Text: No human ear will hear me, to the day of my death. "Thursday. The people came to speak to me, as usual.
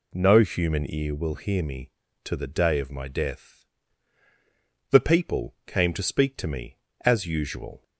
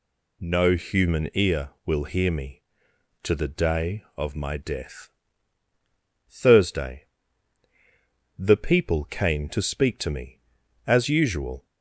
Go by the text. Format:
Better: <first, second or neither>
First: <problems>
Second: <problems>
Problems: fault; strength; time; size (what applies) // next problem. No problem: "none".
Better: second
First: skips "Thursday"; at 4.2 s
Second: none